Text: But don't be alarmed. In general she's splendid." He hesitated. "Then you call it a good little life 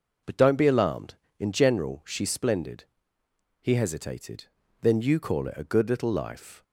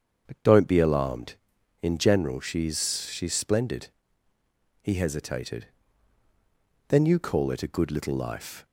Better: first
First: none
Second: starts louder than the rest; strong; until 1.2 s; 7 dB // says "she's" twice; at 3.1 s

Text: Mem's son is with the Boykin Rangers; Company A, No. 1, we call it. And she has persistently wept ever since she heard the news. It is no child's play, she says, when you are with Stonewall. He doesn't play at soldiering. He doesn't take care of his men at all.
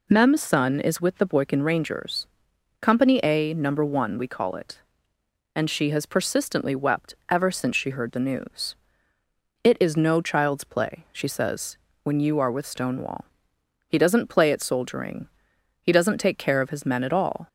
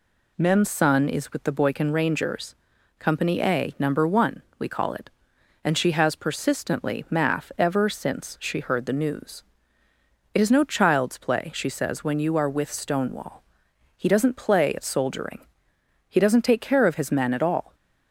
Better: first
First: none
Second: says "math" for "wept"; at 7.0 s

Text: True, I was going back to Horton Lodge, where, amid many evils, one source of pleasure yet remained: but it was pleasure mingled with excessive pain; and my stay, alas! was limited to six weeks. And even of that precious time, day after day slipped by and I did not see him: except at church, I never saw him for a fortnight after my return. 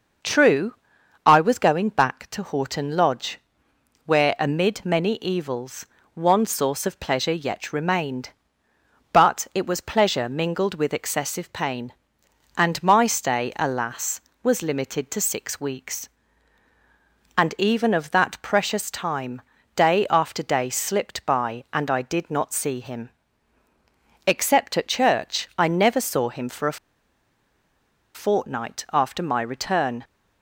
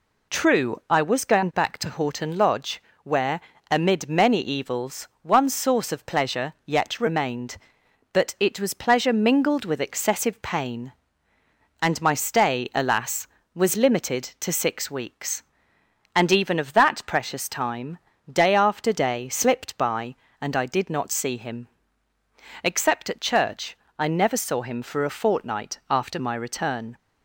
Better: second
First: starts louder than the rest; noticeable; until 1.7 s; 6 dB // pauses between "a" and "fortnight"; strong; at 26.7 s; 1.3 s long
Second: none

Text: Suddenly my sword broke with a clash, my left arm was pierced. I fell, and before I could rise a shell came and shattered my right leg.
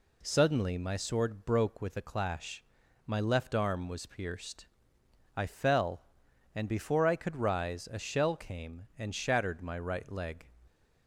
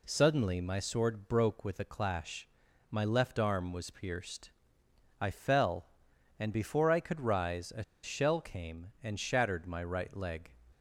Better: first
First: none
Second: pauses between "a" and "shell"; slight; at 7.8 s; 0.20 s long

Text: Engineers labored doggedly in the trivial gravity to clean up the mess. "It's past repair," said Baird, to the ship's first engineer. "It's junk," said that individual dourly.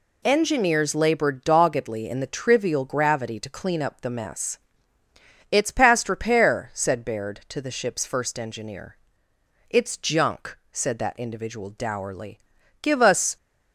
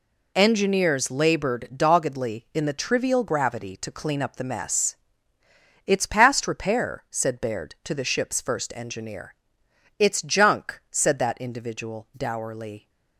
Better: second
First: goes on to say "Give us"; from 12.8 s on; 0.54 s long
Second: none

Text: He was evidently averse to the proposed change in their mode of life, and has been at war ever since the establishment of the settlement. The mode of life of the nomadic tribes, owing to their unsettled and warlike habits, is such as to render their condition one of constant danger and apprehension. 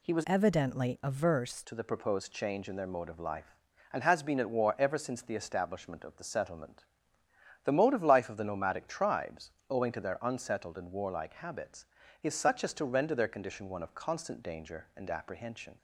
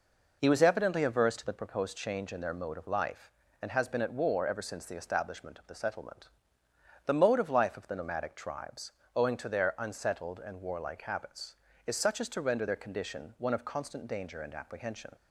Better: second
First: changes voice from "evidently" to "averse"; from 0.2 to 1.6 s; 1.4 s long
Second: none

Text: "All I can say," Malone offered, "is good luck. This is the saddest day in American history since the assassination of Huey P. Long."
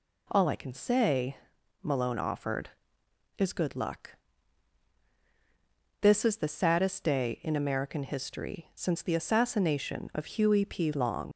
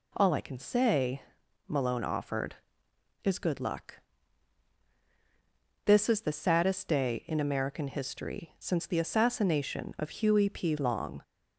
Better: second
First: leaves "Long" unfinished; at 11.3 s; 65 ms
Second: none

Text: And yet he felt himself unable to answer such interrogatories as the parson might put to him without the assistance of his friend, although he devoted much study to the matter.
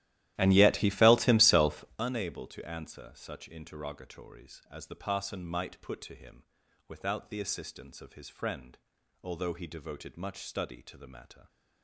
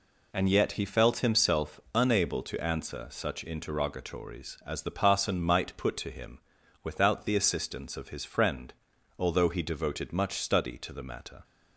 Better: second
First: starts louder than the rest; strong; until 2.0 s; 14 dB // pauses between "himself" and "unable"; slight; at 1.8 s; 0.16 s long // pauses between "him" and "without"; at 6.4 s; 0.44 s long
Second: pauses between "himself" and "unable"; slight; at 1.7 s; 0.16 s long // pauses between "him" and "without"; at 6.3 s; 0.44 s long

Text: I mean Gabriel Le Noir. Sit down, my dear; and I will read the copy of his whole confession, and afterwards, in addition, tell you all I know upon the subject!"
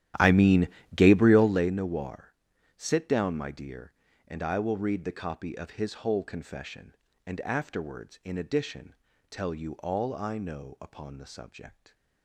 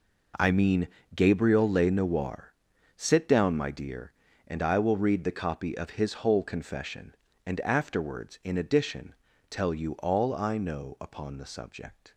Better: second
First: starts louder than the rest; strong; until 1.7 s; 12.5 dB // pauses between "mean" and "Gabriel"; slight; at 0.6 s; 0.26 s long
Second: pauses between "mean" and "Gabriel"; slight; at 0.8 s; 0.26 s long

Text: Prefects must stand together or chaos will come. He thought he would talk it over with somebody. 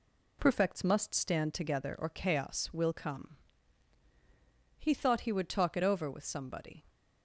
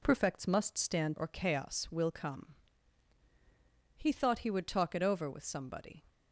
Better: first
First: none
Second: skips "together"; at 1.1 s

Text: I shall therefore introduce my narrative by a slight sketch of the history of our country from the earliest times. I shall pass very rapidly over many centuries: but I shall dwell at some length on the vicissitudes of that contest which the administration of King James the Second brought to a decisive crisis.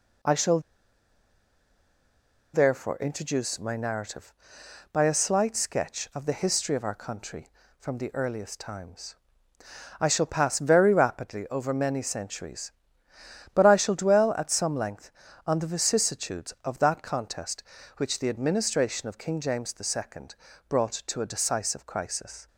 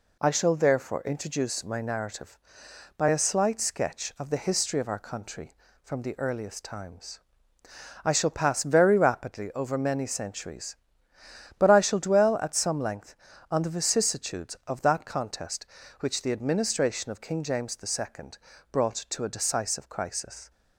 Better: second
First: pauses between "shall" and "therefore"; strong; at 0.5 s; 1.9 s long // pauses between "Second" and "brought"; slight; at 20.3 s; 0.34 s long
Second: pauses between "Second" and "brought"; slight; at 18.3 s; 0.34 s long

